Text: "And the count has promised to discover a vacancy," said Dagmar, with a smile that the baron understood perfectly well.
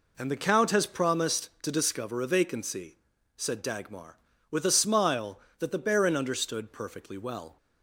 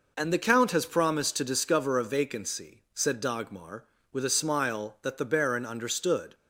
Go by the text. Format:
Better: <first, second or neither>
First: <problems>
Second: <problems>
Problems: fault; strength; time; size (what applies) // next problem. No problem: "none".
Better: first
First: none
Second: stops before "perfectly well"; at 6.3 s